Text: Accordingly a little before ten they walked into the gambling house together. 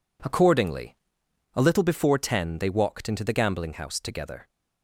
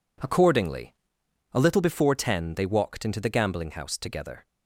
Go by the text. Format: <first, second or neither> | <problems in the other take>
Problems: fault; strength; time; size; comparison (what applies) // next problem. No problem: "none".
neither | pauses between "Accordingly" and "a"; noticeable; the same in both